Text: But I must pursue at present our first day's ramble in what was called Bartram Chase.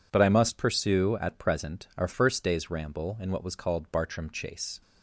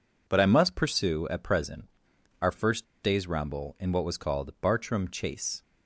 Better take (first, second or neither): first